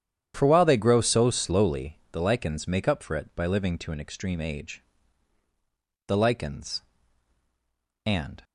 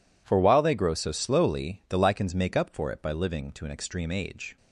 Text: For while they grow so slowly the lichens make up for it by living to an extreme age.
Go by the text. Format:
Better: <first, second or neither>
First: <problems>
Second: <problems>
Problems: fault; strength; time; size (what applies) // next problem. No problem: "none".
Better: second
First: starts louder than the rest; strong; until 1.3 s; 9.5 dB // pauses between "slowly" and "the"; slight; at 1.9 s; 0.16 s long // goes on to say "THE LICHENS AND"; strong; from 6.0 s on; 2.3 s long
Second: none